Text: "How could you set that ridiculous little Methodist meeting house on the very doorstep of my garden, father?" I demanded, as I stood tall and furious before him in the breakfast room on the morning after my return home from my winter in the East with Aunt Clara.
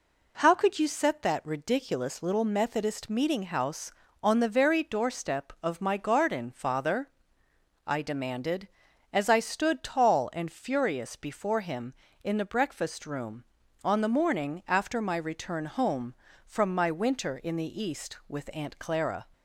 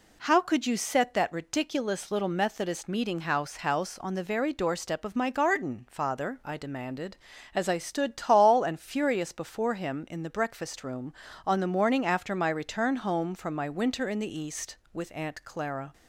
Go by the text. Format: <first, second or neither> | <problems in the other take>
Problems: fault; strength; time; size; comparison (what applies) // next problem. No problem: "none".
first | says "house" twice; at 3.5 s